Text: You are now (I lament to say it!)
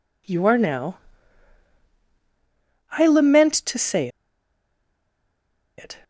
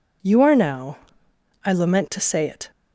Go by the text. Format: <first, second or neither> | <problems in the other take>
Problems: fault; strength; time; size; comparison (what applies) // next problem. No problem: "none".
second | pauses between "say" and "it"; strong; at 4.0 s; 1.7 s long